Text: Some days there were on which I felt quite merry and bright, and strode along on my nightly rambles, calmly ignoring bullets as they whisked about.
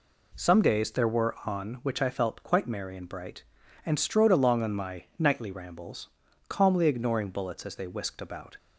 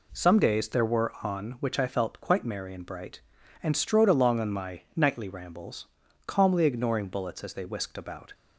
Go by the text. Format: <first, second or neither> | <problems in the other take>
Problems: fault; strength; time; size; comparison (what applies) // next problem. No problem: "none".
neither | none